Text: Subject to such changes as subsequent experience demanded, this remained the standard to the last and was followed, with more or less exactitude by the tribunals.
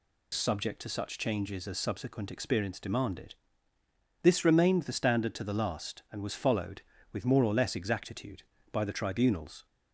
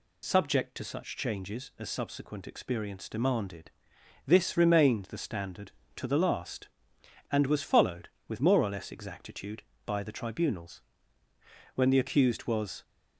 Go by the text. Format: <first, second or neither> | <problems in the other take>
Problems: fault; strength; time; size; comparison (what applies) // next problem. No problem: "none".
first | goes on to say "When the accused was"; noticeable; from 11.7 s on; 1.0 s long